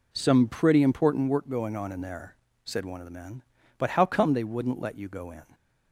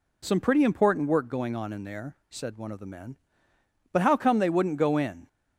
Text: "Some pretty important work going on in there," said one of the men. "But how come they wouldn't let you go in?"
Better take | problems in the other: first | skips "let you"; at 4.7 s

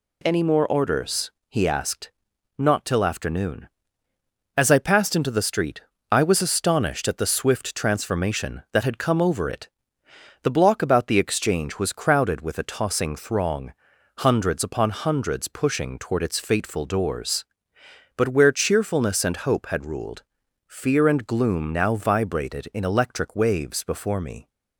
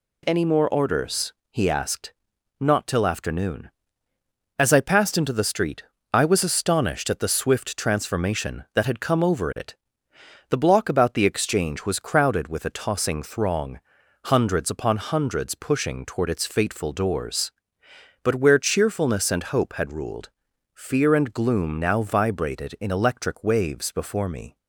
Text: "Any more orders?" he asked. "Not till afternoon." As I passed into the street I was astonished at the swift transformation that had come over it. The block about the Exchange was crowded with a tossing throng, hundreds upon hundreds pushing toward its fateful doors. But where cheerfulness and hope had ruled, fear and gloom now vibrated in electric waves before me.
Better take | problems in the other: neither | pauses between "street" and "I"; slight; the same in both

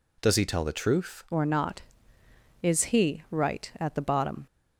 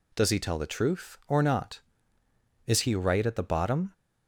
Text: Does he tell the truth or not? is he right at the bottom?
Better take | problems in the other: second | changes voice at "or"; from 1.3 s on; 3.1 s long

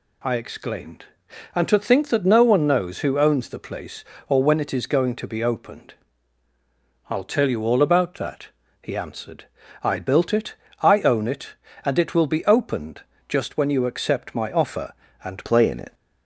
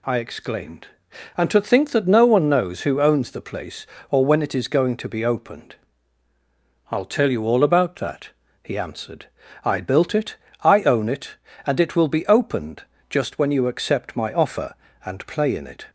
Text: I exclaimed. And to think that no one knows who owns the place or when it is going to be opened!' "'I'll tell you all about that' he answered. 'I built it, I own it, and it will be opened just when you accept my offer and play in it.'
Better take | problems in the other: second | pauses between "that" and "he"; slight; at 8.4 s; 0.32 s long; slight in the second // pauses between "opened" and "just"; slight; at 13.0 s; 0.28 s long; slight in the second // changes voice at "play"; from 15.4 s on; 0.5 s long

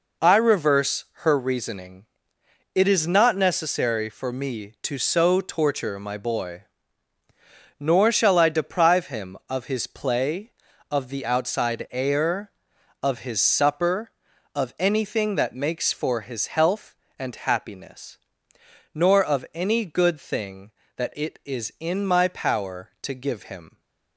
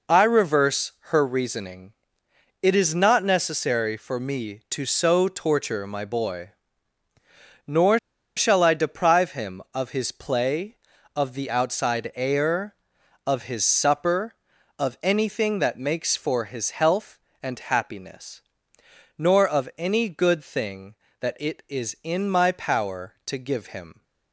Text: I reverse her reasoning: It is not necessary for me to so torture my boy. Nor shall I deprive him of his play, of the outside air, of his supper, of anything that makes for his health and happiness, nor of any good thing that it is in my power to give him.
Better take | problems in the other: first | pauses between "Nor" and "shall"; at 7.9 s; 0.39 s long

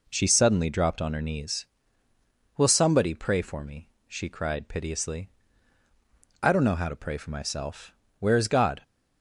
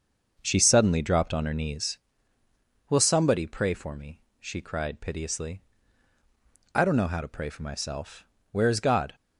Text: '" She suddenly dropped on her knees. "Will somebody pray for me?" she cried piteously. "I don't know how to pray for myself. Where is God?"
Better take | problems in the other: first | starts louder than the rest; noticeable; until 2.0 s; 6 dB

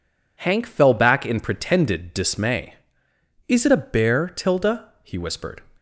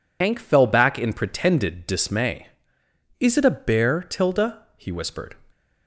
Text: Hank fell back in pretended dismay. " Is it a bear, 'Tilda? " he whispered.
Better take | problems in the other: first | loses the start of "Hank"; at 0.2 s; 80 ms

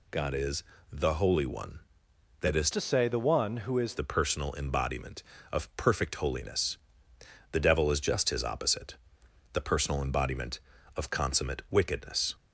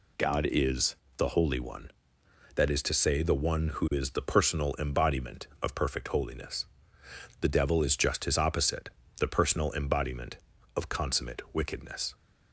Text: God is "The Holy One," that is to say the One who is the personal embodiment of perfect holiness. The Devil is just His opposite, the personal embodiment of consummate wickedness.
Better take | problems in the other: second | pauses between "is" and "The"; slight; at 0.6 s; 0.28 s long; slight in the second // changes voice from "to" to "is"; from 2.7 to 3.9 s; 1.2 s long

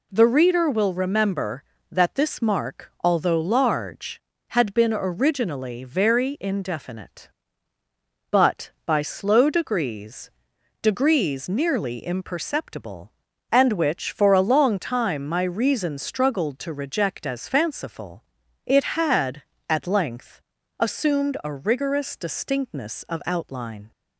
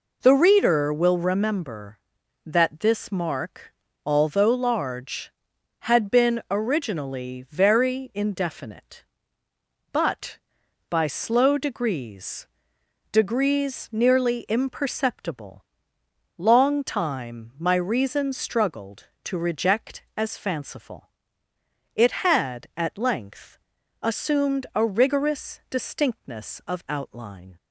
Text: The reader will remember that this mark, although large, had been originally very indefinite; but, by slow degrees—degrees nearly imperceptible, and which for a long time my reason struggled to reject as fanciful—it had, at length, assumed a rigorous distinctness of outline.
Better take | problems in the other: first | skips "and which for a"; at 16.0 s

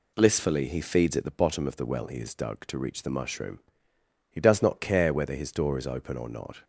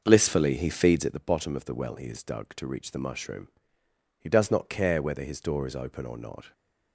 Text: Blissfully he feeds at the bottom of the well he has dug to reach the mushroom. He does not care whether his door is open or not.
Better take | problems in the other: first | starts louder than the rest; noticeable; until 1.1 s; 6 dB

